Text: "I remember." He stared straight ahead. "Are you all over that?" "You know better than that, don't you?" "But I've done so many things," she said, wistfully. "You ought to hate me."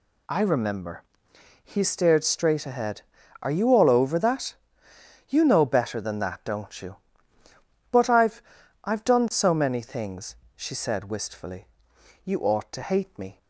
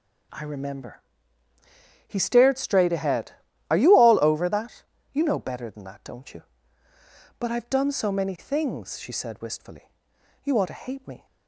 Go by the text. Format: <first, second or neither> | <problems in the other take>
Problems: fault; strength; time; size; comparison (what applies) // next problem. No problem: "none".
second | says "I've" twice; at 8.8 s